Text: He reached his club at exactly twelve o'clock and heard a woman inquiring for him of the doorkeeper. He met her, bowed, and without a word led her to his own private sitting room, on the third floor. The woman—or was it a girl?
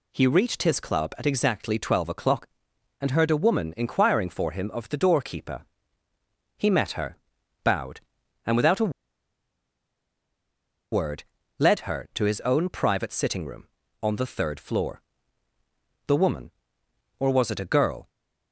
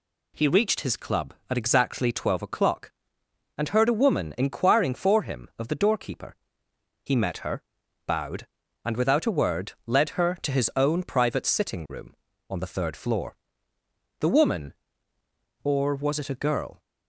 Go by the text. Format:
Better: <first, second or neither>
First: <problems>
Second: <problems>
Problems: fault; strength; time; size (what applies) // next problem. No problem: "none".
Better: second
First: pauses between "a" and "word"; strong; at 8.8 s; 2.0 s long // pauses between "word" and "led"; slight; at 11.2 s; 0.34 s long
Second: none